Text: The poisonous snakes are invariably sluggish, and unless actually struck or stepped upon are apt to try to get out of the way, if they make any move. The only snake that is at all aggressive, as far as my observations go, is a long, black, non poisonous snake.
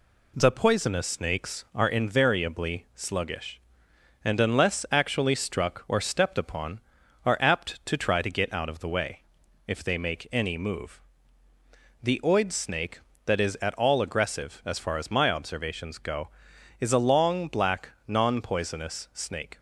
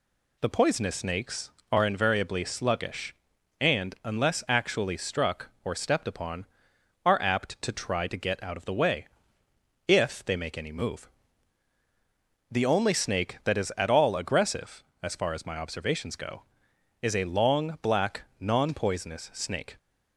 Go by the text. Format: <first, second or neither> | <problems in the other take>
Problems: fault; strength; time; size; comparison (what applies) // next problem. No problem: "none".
second | says "oid" for "only"; at 12.2 s